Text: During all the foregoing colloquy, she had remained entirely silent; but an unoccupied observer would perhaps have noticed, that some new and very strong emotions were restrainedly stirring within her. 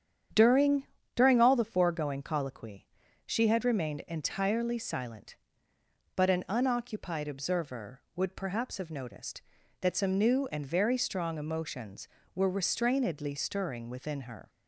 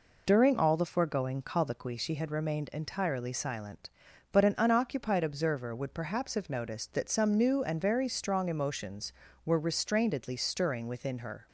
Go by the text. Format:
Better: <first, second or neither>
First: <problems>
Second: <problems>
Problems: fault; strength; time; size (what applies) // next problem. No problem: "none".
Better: second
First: starts louder than the rest; strong; until 1.6 s; 8.5 dB // says "During" twice; at 1.1 s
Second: none